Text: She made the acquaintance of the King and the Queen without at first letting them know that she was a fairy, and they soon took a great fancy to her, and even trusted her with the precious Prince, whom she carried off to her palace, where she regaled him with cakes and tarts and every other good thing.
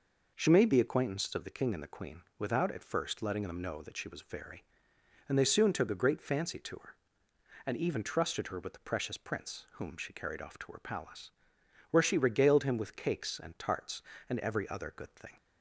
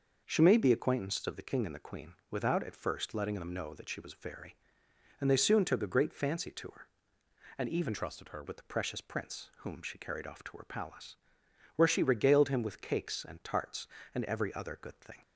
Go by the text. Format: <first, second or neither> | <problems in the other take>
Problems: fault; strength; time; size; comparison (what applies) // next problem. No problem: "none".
first | pauses between "Queen" and "without"; slight; at 2.1 s; 0.16 s long; slight in the first // changes voice from "trusted" to "her"; from 7.9 to 8.4 s; 0.5 s long